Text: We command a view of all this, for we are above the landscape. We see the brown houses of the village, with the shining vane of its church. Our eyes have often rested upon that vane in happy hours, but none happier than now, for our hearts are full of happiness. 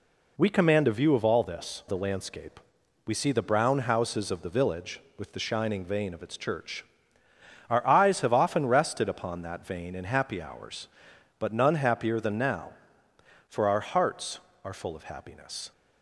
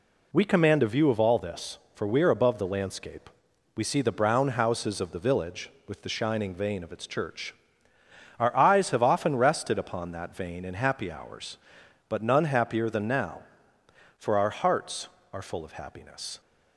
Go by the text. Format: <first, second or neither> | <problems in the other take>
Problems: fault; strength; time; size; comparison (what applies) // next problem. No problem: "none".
second | skips "for we are above"; at 1.8 s